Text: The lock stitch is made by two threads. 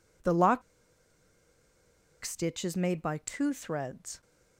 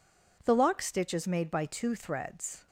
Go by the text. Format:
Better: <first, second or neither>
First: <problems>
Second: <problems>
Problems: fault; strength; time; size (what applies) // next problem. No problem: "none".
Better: second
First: pauses between "lock" and "stitch"; strong; at 0.6 s; 1.6 s long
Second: none